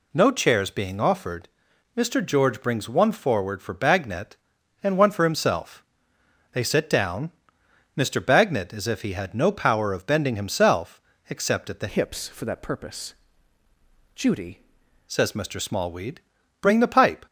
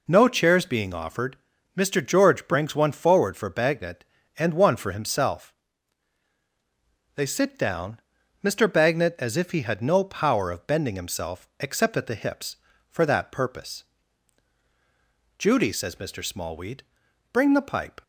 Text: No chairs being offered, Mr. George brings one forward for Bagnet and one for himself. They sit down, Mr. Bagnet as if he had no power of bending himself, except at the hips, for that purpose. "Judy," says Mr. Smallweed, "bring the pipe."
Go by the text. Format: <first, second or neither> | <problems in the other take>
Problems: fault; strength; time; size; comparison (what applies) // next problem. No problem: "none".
second | changes voice from "hips" to "Judy"; from 11.8 to 14.5 s; 2.7 s long